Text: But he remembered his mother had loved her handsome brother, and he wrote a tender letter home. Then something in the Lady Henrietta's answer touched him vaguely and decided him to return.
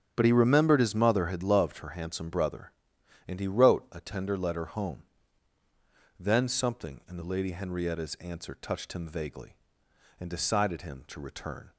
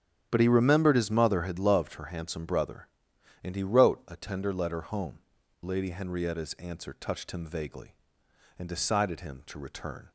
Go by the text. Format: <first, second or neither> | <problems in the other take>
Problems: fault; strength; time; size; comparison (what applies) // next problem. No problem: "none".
first | starts louder than the rest; strong; until 1.3 s; 9.5 dB; strong in the first // skips "Then something in the"; at 5.4 s